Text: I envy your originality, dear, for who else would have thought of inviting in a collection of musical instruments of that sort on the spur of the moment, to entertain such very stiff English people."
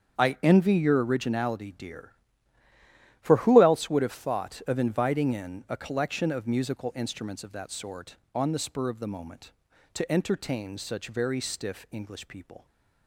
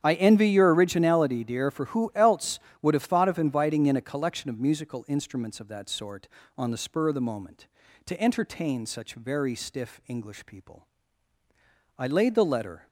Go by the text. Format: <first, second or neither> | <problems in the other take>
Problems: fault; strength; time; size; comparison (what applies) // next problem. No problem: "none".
first | starts louder than the rest; strong; until 1.0 s; 9 dB; strong in the first // goes on to say "I laid the letter"; noticeable; from 11.9 s on; 0.89 s long